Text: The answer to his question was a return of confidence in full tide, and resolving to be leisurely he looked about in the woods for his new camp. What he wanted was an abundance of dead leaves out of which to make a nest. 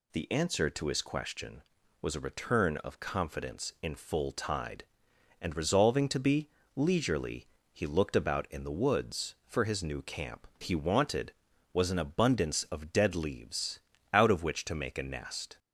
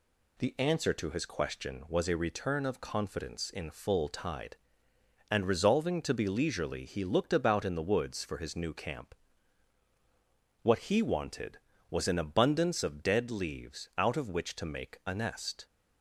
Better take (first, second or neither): second